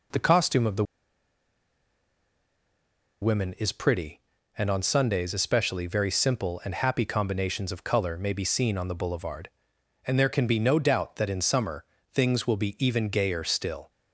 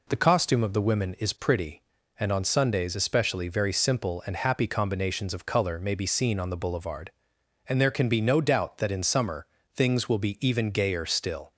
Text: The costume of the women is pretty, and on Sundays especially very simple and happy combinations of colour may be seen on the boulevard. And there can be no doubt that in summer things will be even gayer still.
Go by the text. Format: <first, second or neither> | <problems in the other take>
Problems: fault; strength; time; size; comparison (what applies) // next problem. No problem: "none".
second | pauses between "the" and "women"; strong; at 0.8 s; 2.3 s long // pauses between "summer" and "things"; slight; at 11.8 s; 0.30 s long; slight in the second